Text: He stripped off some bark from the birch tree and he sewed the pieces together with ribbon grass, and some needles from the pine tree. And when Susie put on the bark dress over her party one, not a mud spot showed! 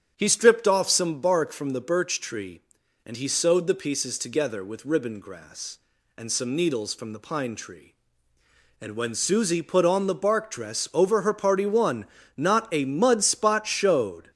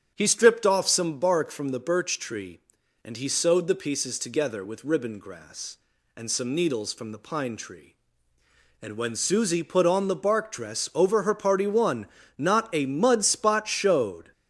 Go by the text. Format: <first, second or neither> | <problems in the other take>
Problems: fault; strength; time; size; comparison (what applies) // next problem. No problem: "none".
neither | starts louder than the rest; strong; the same in both